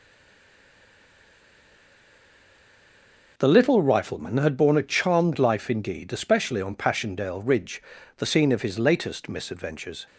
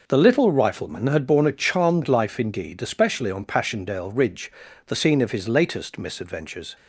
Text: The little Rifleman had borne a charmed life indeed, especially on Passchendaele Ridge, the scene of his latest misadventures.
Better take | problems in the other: second | stays silent before the first word; strong; until 3.3 s; 3.3 s long

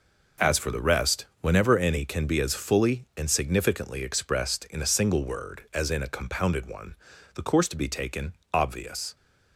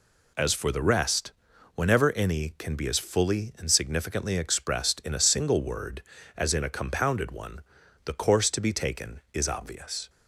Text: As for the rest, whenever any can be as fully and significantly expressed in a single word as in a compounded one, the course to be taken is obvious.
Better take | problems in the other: second | skips "is"; at 8.4 s

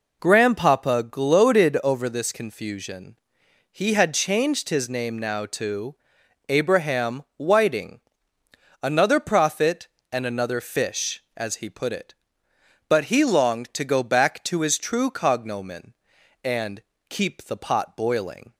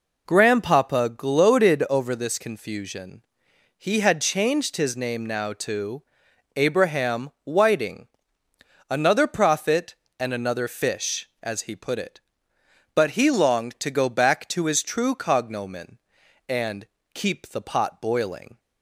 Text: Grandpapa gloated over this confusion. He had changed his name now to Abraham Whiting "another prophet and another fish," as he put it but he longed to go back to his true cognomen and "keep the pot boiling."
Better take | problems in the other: neither | pauses between "to" and "Abraham"; noticeable; the same in both // pauses between "Whiting" and "another"; noticeable; the same in both // pauses between "and" and "keep"; slight; the same in both

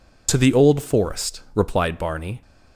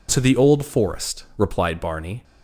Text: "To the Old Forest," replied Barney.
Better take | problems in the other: second | loses the start of "To"; at 0.2 s; 30 ms

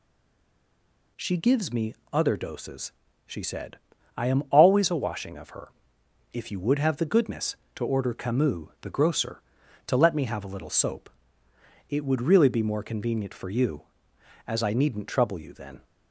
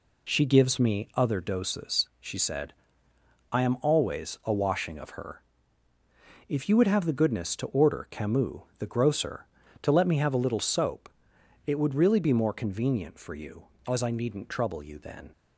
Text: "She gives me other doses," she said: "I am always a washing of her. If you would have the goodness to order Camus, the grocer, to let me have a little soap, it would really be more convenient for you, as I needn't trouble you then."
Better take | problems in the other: second | stays silent before the first word; noticeable; until 1.1 s; 1.1 s long // pauses between "me" and "other"; slight; at 1.9 s; 0.18 s long

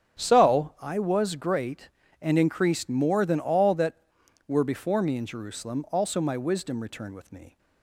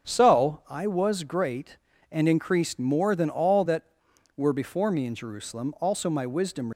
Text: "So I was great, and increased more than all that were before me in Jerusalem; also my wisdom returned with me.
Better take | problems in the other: first | starts louder than the rest; until 1.1 s; 6.5 dB; strong in the first // stops before "returned with me"; at 6.7 s

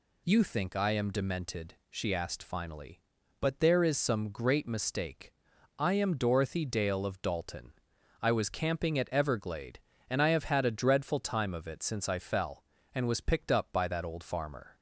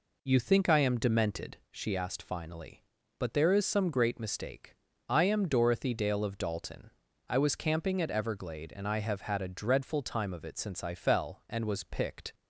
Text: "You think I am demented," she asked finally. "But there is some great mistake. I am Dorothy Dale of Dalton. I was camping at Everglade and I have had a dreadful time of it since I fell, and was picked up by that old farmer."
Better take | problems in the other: first | stops before "up by that old farmer"; at 12.3 s

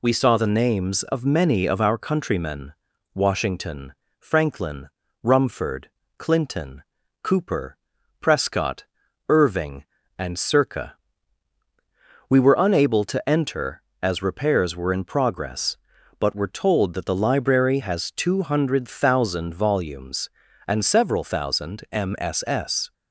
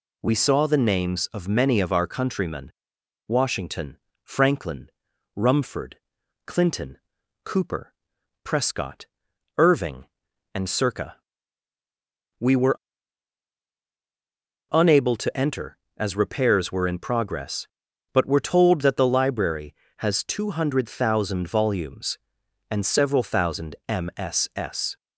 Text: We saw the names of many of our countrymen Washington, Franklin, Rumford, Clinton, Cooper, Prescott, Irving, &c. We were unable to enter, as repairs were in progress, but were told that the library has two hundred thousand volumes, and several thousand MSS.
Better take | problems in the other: first | pauses between "countrymen" and "Washington"; noticeable; at 2.7 s; 0.56 s long; also in the first // pauses between "were" and "unable"; strong; at 12.7 s; 1.9 s long

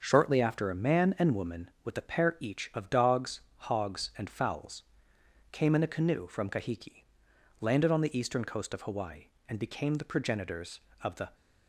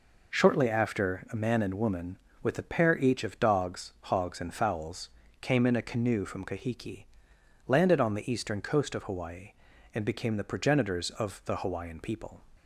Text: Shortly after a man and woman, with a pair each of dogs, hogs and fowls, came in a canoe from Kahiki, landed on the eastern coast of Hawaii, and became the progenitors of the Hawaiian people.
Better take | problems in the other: second | starts louder than the rest; until 1.0 s; 6.5 dB // stops before "Hawaiian people"; at 11.3 s

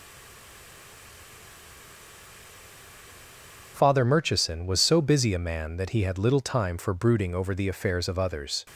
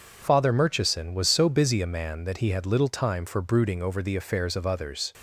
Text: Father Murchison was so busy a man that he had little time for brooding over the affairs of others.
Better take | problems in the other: second | stays silent before the first word; strong; until 3.7 s; 3.7 s long

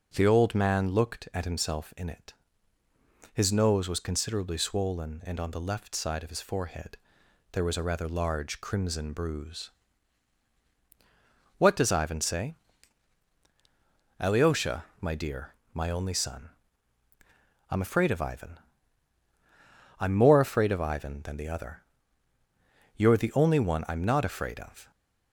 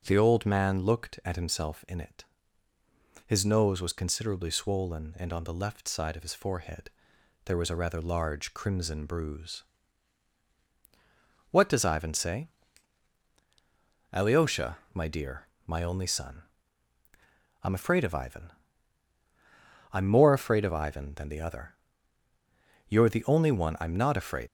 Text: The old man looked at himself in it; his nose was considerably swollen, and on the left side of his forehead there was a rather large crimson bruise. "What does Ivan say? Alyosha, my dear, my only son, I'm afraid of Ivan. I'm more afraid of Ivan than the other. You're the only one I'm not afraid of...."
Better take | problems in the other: first | pauses between "forehead" and "there"; noticeable; at 6.8 s; 0.56 s long; noticeable in the first // stops before "of"; at 24.4 s

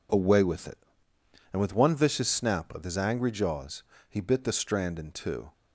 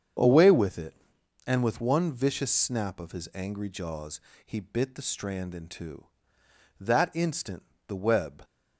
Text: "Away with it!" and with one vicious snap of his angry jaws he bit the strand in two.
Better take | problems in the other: first | starts louder than the rest; strong; until 1.6 s; 7.5 dB // pauses between "jaws" and "he"; slight; at 4.1 s; 0.24 s long; slight in the first // goes on to say "That instant the web"; from 6.8 s on; 1.6 s long

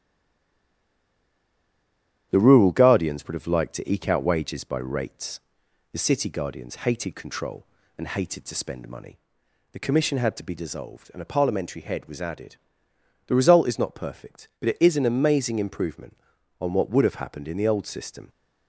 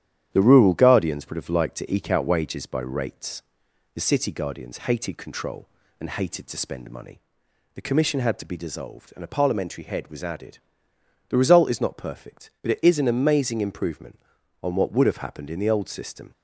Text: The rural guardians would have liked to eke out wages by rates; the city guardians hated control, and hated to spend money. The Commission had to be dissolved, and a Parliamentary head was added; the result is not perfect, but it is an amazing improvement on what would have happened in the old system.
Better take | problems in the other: second | stays silent before the first word; until 2.3 s; 2.3 s long // starts louder than the rest; strong; until 3.3 s; 10.5 dB; strong in the second

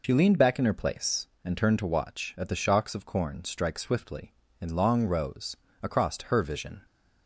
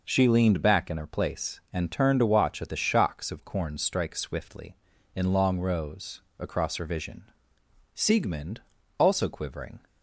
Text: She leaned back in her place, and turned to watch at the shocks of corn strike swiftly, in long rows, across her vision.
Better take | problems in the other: first | goes on to say "Siegmund also quivering"; strong; from 7.9 s on; 1.8 s long

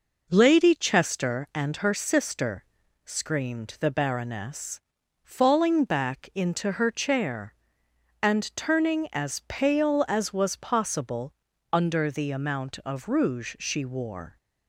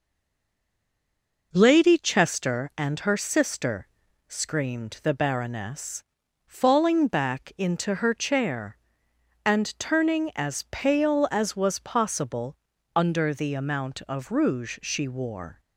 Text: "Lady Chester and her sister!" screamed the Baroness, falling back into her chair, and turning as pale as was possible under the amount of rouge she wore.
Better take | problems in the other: first | stays silent before the first word; noticeable; until 1.5 s; 1.5 s long // pauses between "possible" and "under"; at 12.5 s; 0.38 s long; also in the first

